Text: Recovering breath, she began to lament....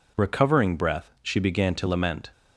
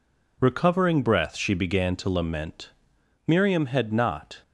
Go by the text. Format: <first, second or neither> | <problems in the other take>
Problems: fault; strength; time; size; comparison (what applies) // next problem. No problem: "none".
first | goes on to say "Miriam had not"; noticeable; from 3.2 s on; 1.1 s long